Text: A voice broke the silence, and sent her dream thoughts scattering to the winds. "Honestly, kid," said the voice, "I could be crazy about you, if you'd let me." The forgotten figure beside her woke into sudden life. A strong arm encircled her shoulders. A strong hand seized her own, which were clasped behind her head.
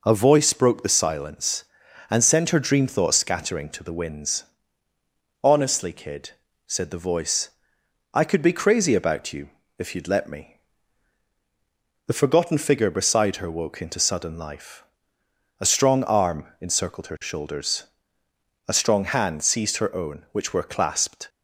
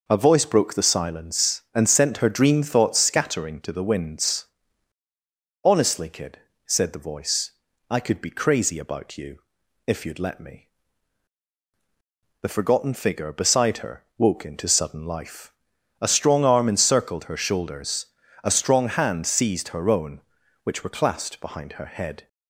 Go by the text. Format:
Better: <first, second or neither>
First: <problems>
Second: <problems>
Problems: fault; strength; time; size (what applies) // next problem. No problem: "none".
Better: second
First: stops before "behind her head"; at 21.2 s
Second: none